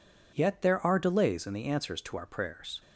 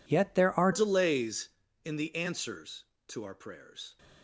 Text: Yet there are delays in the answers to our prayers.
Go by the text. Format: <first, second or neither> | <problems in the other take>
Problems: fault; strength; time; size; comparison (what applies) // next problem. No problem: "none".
first | changes voice at "delays"; from 0.7 s on; 3.2 s long